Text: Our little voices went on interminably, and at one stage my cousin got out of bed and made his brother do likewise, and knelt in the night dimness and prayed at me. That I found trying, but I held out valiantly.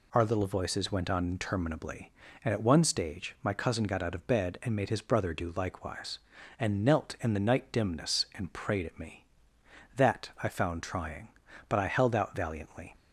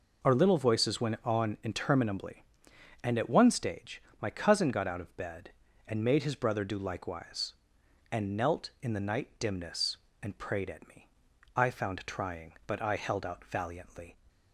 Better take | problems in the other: first | pauses between "stage" and "my"; slight; at 4.0 s; 0.18 s long // skips "That"; at 11.3 s

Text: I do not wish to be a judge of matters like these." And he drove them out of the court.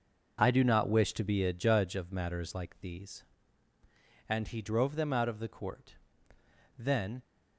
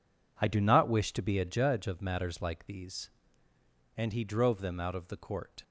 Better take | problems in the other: second | goes on to say "Then"; slight; from 6.7 s on; 0.44 s long

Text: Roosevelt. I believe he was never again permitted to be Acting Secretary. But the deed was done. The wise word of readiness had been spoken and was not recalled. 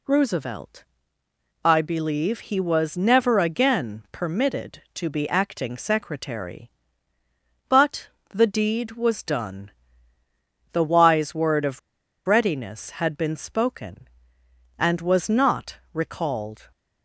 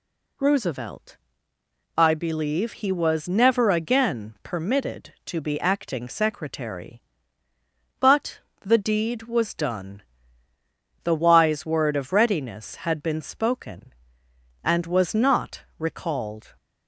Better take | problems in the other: second | pauses between "But" and "the"; slight; at 8.0 s; 0.20 s long; slight in the second // pauses between "of" and "readiness"; noticeable; at 11.7 s; 0.47 s long // pauses between "not" and "recalled"; slight; at 15.7 s; 0.16 s long; slight in the second

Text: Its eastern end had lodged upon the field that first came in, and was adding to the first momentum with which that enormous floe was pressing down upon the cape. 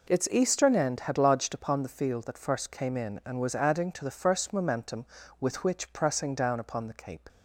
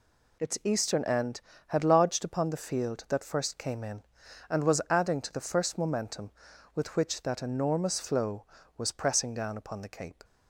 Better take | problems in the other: second | skips "that enormous floe was"; at 5.9 s

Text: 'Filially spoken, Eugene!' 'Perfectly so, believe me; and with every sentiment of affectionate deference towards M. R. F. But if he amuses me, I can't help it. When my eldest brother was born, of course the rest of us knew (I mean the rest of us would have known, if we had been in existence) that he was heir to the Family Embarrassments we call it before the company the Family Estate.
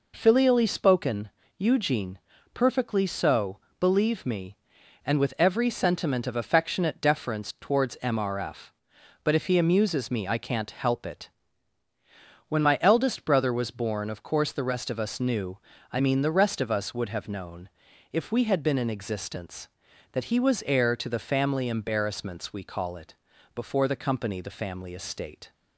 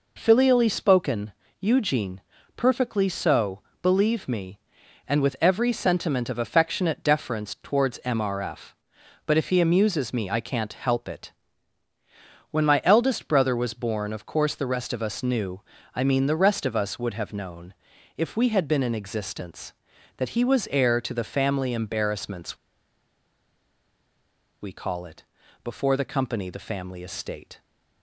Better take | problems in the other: first | pauses between "Embarrassments" and "we"; strong; at 22.5 s; 2.0 s long // pauses between "it" and "before"; at 25.2 s; 0.40 s long; also in the first

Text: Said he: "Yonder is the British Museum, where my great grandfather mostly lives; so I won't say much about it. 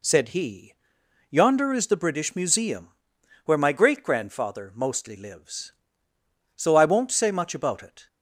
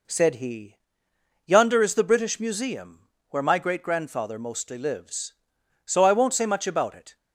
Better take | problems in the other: neither | none

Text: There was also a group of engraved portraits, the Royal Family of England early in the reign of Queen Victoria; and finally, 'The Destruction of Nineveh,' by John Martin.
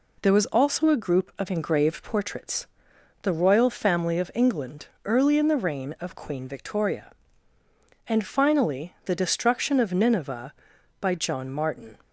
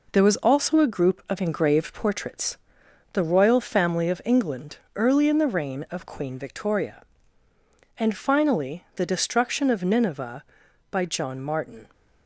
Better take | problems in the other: first | gets quieter; noticeable; throughout; 5 dB // pauses between "England" and "early"; slight; at 4.7 s; 0.18 s long; slight in the first

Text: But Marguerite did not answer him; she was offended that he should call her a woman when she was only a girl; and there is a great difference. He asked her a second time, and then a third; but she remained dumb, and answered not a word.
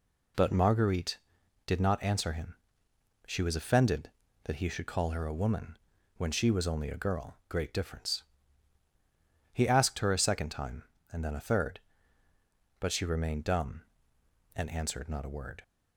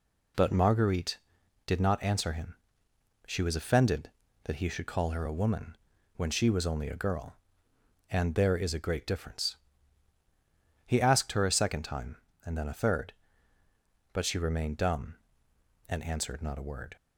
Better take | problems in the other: second | pauses between "woman" and "when"; at 5.7 s; 0.38 s long; also in the second // skips "and there is a"; at 7.4 s

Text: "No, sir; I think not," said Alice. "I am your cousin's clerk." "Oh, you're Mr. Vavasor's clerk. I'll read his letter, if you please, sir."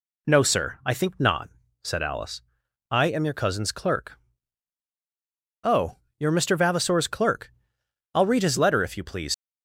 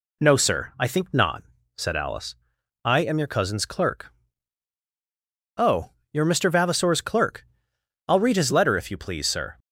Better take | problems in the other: second | stops before "sir"; at 9.3 s

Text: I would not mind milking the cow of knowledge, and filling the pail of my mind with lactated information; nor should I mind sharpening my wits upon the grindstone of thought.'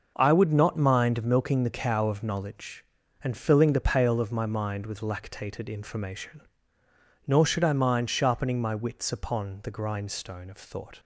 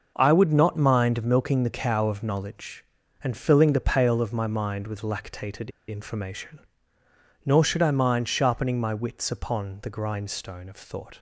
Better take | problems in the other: first | pauses between "lactated" and "information"; slight; at 5.7 s; 0.19 s long

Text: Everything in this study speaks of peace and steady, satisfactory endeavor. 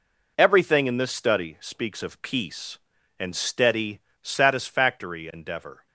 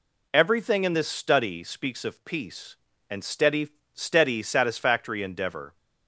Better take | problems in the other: first | says "steady" twice; at 3.9 s

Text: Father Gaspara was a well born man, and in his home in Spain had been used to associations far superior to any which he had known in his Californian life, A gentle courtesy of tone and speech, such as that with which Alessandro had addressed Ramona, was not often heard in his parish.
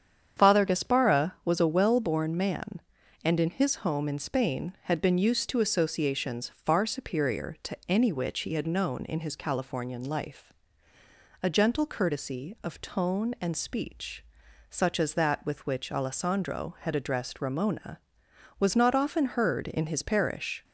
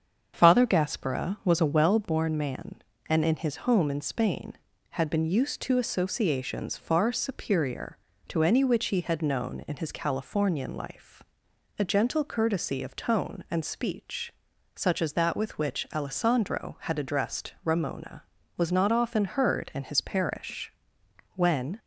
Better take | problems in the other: first | starts louder than the rest; strong; until 1.3 s; 7.5 dB; strong in the first // goes on to say "When"; slight; from 21.3 s on; 0.42 s long

